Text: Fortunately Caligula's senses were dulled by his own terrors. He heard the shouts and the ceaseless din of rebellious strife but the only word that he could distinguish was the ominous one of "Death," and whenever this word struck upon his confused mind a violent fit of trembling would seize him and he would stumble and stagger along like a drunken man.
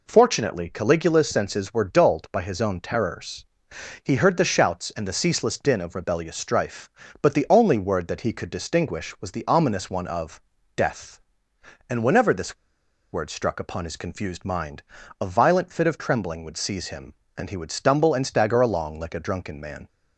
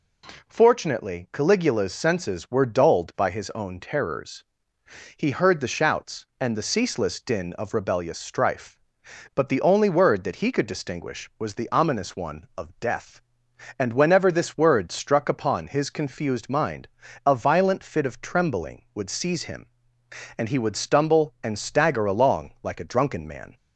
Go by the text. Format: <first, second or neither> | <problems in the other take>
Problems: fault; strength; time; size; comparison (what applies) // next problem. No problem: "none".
second | pauses between "of" and "Death"; slight; at 10.4 s; 0.36 s long // pauses between "this" and "word"; noticeable; at 12.5 s; 0.55 s long // pauses between "mind" and "a"; slight; at 14.8 s; 0.36 s long; slight in the second